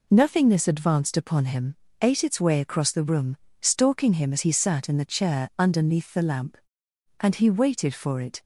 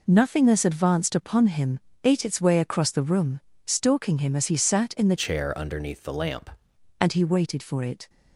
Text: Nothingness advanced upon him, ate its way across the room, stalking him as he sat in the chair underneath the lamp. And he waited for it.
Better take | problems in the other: first | changes voice from "chair" to "lamp"; from 5.1 to 6.5 s; 1.4 s long

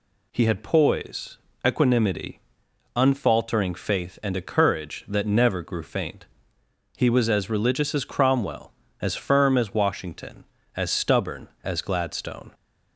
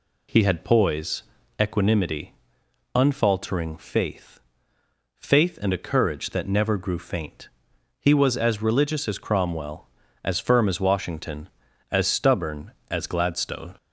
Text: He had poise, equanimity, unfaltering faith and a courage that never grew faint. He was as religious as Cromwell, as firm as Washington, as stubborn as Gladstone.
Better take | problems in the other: first | says "faith" twice; at 5.1 s

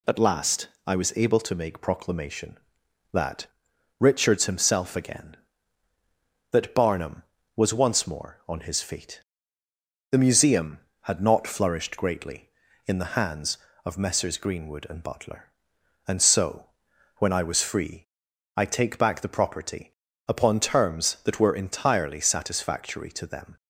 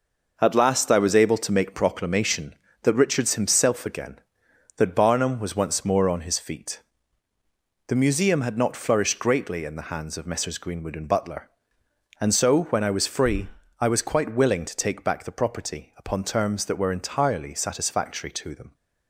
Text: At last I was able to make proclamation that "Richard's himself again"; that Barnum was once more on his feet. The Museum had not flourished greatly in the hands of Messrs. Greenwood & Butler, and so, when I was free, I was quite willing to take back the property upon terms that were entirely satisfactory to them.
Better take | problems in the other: second | pauses between "last" and "I"; slight; at 0.6 s; 0.18 s long // pauses between "that" and "Richard's"; noticeable; at 3.4 s; 0.54 s long // skips "was quite willing to"; at 18.6 s // pauses between "property" and "upon"; slight; at 19.9 s; 0.34 s long

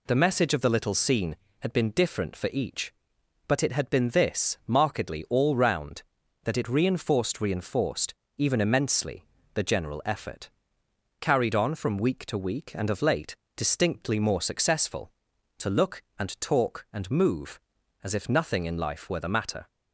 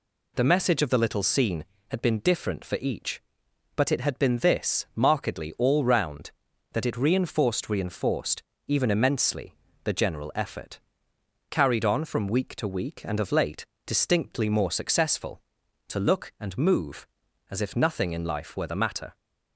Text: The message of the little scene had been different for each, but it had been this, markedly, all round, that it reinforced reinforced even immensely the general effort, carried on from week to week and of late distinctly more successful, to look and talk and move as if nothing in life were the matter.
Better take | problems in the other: first | pauses between "reinforced" and "even"; slight; at 8.4 s; 0.28 s long; slight in the first // pauses between "immensely" and "the"; slight; at 9.5 s; 0.28 s long; slight in the first // pauses between "late" and "distinctly"; slight; at 13.6 s; 0.20 s long; slight in the first // skips "and talk"; at 16.3 s

